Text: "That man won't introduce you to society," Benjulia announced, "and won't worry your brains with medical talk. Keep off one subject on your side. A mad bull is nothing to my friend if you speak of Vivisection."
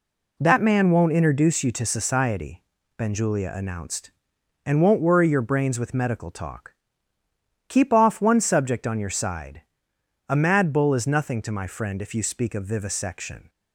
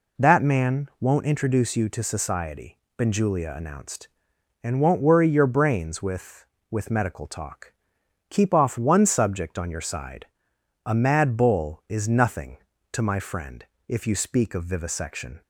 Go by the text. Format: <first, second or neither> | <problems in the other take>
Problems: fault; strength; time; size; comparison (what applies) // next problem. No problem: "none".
first | says "with" twice; at 6.6 s // pauses between "friend" and "if"; slight; at 13.6 s; 0.24 s long